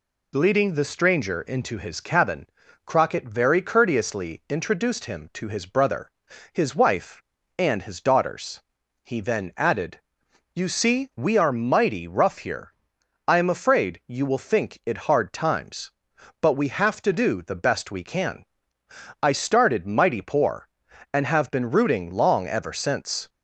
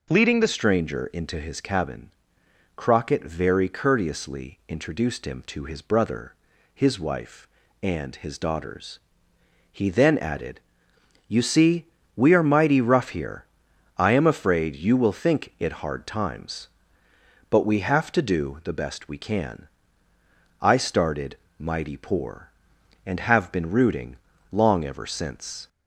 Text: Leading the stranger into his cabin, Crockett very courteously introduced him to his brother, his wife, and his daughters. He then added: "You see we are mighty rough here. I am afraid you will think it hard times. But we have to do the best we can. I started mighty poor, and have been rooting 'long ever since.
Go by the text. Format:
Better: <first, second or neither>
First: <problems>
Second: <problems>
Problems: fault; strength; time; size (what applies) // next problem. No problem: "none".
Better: first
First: none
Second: changes voice at "stranger"; from 0.4 s on; 25.2 s long // pauses between "see" and "we"; slight; at 11.8 s; 0.28 s long // pauses between "started" and "mighty"; slight; at 21.3 s; 0.22 s long // pauses between "rooting" and "long"; slight; at 24.1 s; 0.36 s long